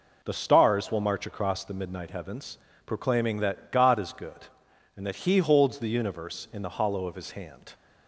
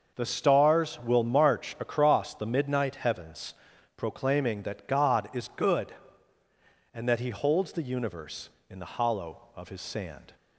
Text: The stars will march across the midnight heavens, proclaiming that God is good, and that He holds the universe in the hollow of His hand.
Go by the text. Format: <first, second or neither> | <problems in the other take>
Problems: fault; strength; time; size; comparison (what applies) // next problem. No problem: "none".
first | starts louder than the rest; until 1.1 s; 6.5 dB // says "sand" for "hand"; at 9.8 s